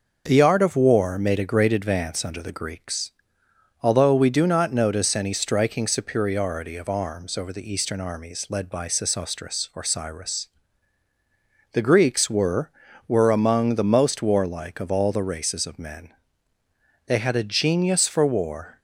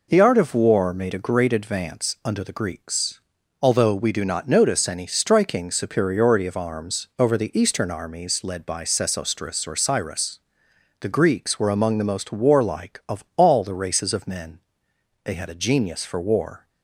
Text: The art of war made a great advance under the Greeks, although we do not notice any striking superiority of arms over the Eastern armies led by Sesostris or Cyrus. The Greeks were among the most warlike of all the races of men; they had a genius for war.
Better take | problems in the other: second | says "were" twice; at 13.0 s

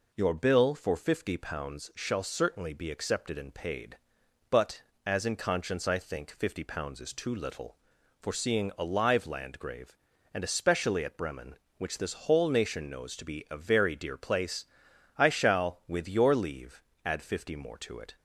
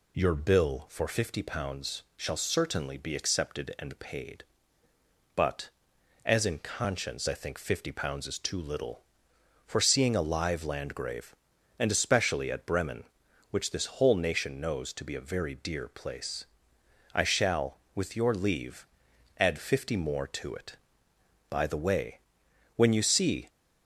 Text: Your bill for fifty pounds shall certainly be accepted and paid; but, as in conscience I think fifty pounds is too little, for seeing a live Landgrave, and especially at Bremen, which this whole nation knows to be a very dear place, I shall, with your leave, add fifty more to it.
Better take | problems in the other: first | goes on to say "By the way when you see"; strong; from 21.5 s on; 1.9 s long

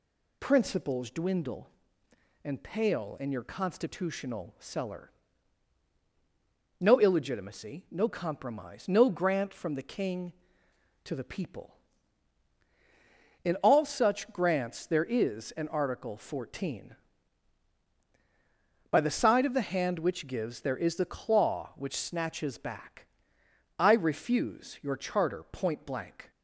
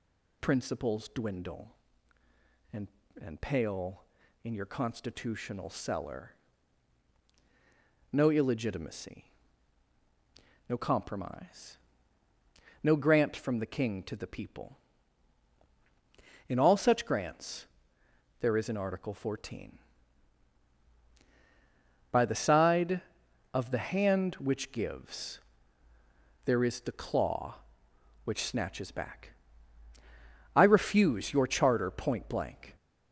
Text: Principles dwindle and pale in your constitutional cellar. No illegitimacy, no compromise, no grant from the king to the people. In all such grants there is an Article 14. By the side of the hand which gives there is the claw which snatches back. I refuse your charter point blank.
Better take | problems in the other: first | says "and" twice; at 3.2 s // pauses between "grants" and "there"; noticeable; at 17.6 s; 0.74 s long // pauses between "gives" and "there"; at 25.3 s; 1.0 s long

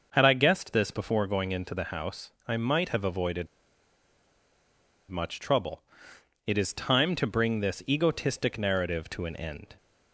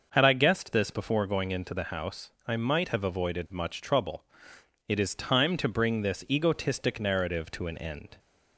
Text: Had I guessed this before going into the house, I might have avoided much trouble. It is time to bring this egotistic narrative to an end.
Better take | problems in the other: second | starts louder than the rest; noticeable; until 1.1 s; 6 dB; noticeable in the second // pauses between "avoided" and "much"; strong; at 3.4 s; 1.6 s long

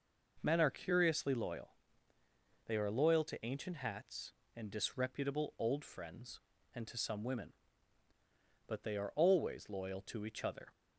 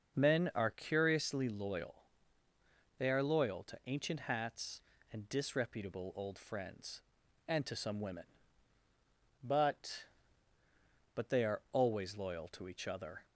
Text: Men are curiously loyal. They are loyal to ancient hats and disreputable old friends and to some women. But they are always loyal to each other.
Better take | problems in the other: first | starts louder than the rest; noticeable; until 1.2 s; 6 dB // says "But" twice; at 11.1 s

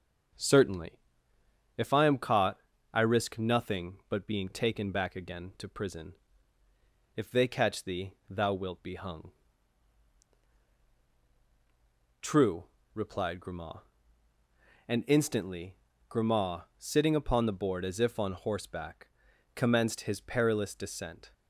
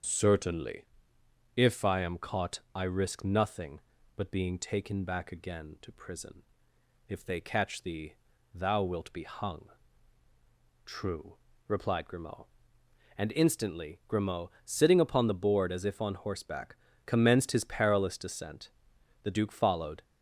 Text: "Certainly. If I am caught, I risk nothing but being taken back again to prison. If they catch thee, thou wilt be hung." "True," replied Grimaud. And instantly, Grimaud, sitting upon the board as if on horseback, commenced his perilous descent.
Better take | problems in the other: first | starts louder than the rest; until 1.7 s; 6.5 dB; also in the first // goes on to say "The duke followed"; noticeable; from 19.2 s on; 0.80 s long

